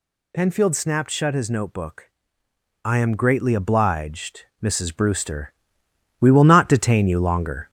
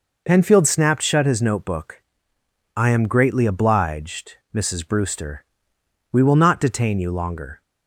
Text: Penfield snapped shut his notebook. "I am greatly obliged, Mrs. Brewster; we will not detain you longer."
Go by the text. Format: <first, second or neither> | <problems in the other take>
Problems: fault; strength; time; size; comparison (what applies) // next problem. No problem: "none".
second | gets louder; throughout; 4 dB